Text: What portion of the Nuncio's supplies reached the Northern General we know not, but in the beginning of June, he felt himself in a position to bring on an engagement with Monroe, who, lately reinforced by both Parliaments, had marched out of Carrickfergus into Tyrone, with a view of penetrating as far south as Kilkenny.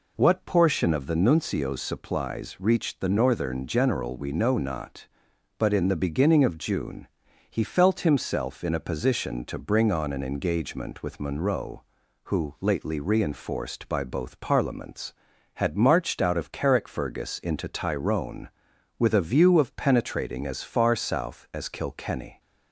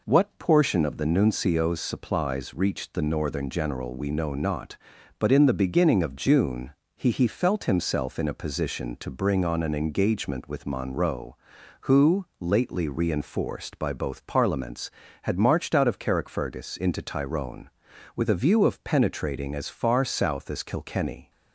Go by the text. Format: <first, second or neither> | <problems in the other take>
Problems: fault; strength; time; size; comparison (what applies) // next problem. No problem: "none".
first | says "he" twice; at 7.0 s